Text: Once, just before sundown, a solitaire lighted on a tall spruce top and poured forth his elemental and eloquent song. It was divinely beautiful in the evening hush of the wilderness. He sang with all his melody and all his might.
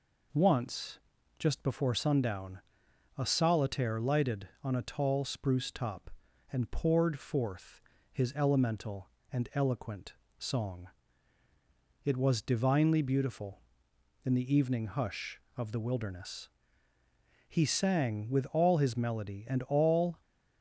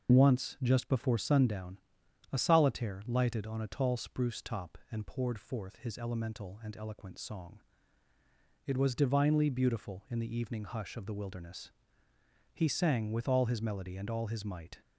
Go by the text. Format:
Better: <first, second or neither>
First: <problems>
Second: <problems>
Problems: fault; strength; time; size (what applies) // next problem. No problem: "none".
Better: second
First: pauses between "forth" and "his"; slight; at 7.8 s; 0.32 s long // pauses between "eloquent" and "song"; slight; at 10.1 s; 0.26 s long // stops before "his might"; at 20.2 s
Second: none